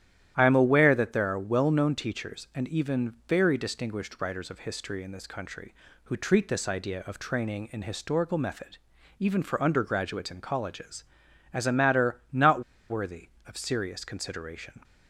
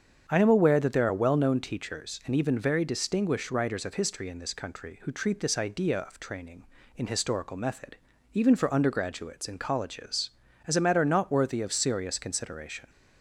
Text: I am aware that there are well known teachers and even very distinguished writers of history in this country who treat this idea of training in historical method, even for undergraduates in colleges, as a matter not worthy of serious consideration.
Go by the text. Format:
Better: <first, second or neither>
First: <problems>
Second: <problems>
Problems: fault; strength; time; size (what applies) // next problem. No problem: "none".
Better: second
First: starts louder than the rest; strong; until 1.3 s; 11.5 dB // pauses between "not" and "worthy"; slight; at 12.6 s; 0.29 s long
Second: starts louder than the rest; strong; until 1.3 s; 7.5 dB